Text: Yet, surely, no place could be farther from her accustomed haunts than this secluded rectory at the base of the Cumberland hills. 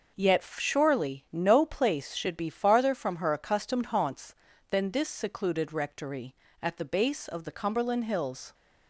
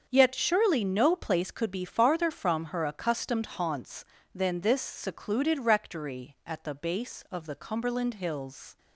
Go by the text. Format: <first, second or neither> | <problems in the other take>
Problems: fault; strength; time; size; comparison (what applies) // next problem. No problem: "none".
second | starts louder than the rest; noticeable; until 1.3 s; 6 dB; also in the second // says "should" for "could"; at 2.1 s